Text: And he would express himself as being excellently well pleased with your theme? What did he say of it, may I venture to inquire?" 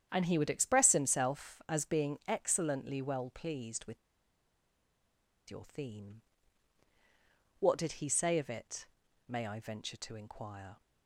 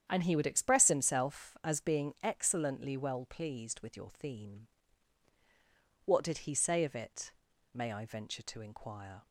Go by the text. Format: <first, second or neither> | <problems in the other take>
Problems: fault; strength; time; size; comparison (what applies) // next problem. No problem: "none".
second | starts louder than the rest; strong; until 1.1 s; 9 dB; strong in the second // pauses between "with" and "your"; strong; at 3.9 s; 1.5 s long